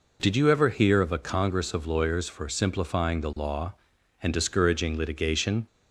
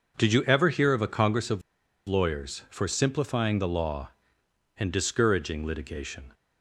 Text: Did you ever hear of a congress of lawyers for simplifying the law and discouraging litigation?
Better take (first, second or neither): first